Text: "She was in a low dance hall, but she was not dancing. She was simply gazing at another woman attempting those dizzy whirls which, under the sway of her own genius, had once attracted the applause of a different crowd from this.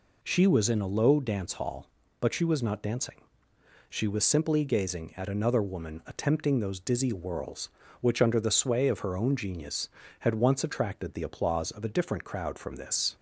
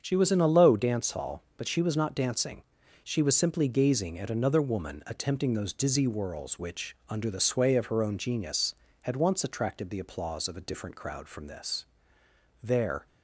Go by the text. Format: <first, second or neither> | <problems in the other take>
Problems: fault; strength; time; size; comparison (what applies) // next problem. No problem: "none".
first | starts louder than the rest; strong; until 1.0 s; 7 dB // goes on to say "There"; slight; from 12.6 s on; 0.44 s long